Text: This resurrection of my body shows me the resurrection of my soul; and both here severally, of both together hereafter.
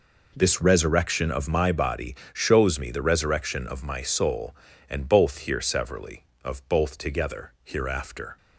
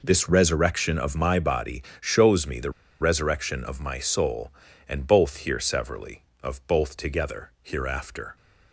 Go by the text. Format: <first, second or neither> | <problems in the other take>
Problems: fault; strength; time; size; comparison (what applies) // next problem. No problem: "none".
first | pauses between "body" and "shows"; slight; at 1.8 s; 0.16 s long; slight in the first // pauses between "the" and "resurrection"; slight; at 2.7 s; 0.29 s long